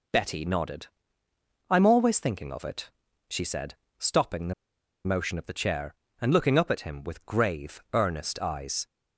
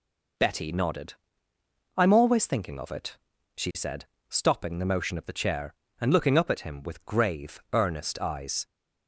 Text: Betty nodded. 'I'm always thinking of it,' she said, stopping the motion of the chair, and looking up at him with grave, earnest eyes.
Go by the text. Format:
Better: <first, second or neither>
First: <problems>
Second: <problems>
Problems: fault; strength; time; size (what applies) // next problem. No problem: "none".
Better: second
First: pauses between "the" and "motion"; noticeable; at 4.5 s; 0.52 s long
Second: none